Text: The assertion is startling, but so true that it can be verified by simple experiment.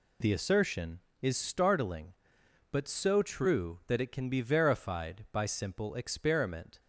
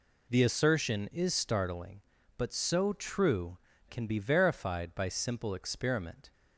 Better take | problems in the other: first | skips "that it"; at 3.7 s

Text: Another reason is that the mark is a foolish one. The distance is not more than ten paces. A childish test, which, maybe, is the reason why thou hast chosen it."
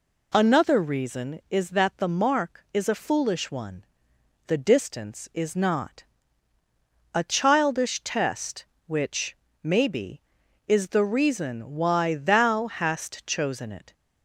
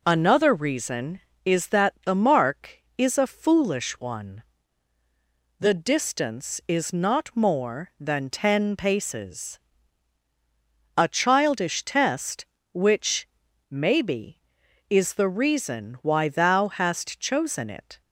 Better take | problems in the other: second | skips "more than ten paces"; at 6.5 s

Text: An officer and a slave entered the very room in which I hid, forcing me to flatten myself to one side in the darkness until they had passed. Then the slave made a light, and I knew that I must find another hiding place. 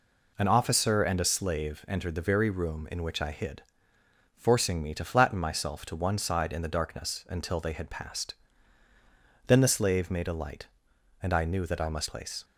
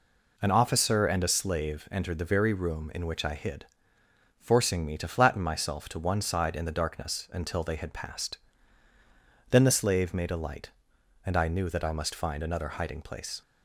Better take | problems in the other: second | skips "find another hiding"; at 12.0 s

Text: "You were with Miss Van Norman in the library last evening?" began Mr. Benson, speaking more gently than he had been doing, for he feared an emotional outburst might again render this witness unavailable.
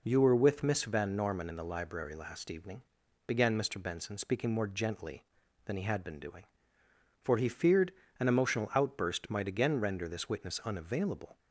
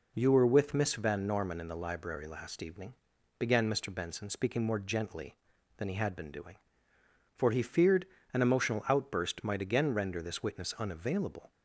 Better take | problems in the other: neither | pauses between "feared" and "an"; slight; the same in both

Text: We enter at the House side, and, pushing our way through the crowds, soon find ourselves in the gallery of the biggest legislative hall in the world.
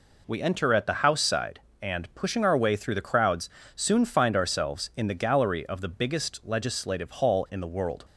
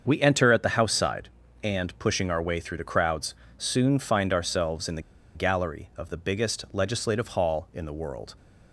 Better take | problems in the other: first | starts louder than the rest; until 1.0 s; 6.5 dB // pauses between "the" and "gallery"; slight; at 5.0 s; 0.33 s long

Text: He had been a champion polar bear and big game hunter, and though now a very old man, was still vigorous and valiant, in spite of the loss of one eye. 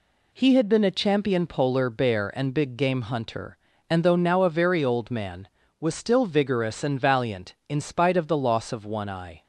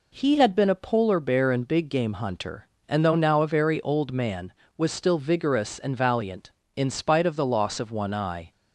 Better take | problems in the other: first | skips "champion"; at 0.7 s

